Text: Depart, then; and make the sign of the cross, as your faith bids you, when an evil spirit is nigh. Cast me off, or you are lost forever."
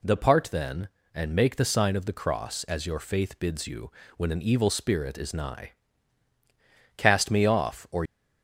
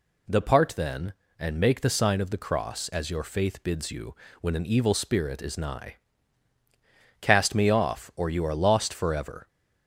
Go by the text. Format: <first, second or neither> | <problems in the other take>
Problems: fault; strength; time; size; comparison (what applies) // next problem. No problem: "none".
second | stops before "you are lost forever"; at 8.0 s